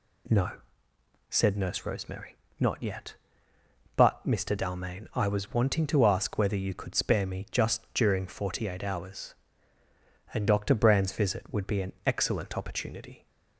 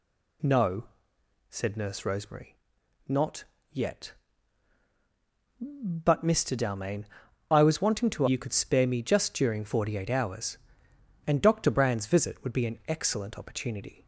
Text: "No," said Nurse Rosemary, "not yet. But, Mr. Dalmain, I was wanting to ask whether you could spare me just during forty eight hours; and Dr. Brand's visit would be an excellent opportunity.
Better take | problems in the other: first | pauses between "not" and "yet"; slight; at 3.4 s; 0.26 s long // skips "ask whether"; at 8.2 s

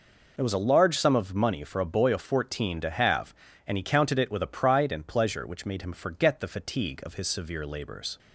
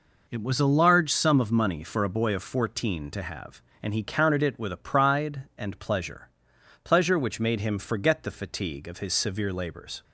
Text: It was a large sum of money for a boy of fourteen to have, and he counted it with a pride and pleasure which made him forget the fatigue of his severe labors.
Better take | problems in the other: first | says "pleasure" twice; at 6.8 s

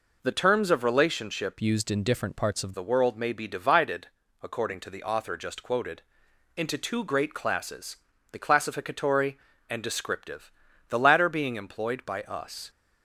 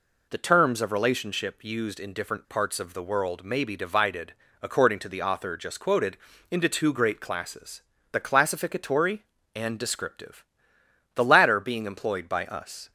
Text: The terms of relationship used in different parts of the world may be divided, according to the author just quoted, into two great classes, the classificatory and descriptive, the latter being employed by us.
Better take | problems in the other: second | changes voice from "used" to "of"; from 1.6 to 2.7 s; 1.1 s long

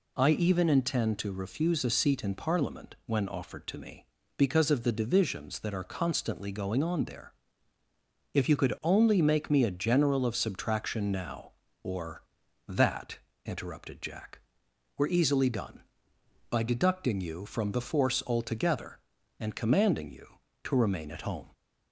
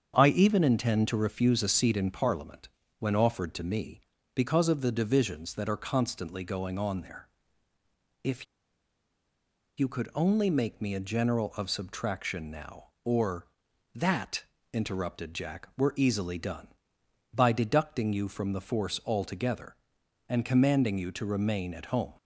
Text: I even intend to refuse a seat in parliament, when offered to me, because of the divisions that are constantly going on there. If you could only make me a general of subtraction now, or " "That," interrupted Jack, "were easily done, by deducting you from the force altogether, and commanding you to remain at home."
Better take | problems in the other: first | starts louder than the rest; strong; until 1.1 s; 7.5 dB // pauses between "If" and "you"; strong; at 8.4 s; 1.3 s long

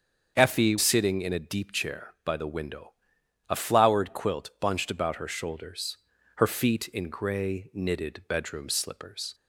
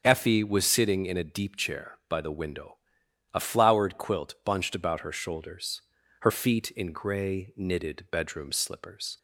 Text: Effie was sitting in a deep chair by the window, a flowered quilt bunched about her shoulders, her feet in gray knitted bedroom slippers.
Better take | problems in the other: second | starts louder than the rest; strong; until 1.4 s; 7 dB; strong in the second // skips "was"; at 0.7 s

